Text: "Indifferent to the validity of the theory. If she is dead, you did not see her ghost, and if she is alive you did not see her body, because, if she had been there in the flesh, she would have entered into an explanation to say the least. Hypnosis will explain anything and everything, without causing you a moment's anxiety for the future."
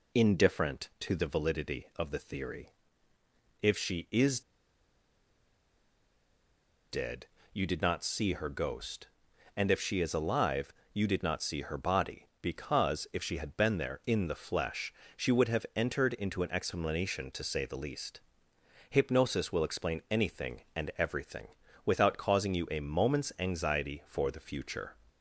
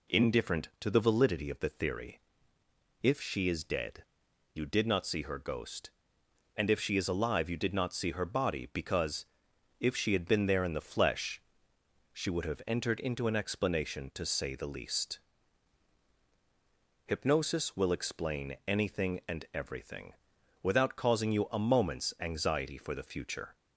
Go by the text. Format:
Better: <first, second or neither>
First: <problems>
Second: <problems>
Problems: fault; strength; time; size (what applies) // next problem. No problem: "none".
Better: second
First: pauses between "is" and "dead"; strong; at 4.4 s; 2.5 s long // pauses between "alive" and "you"; slight; at 10.7 s; 0.22 s long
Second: none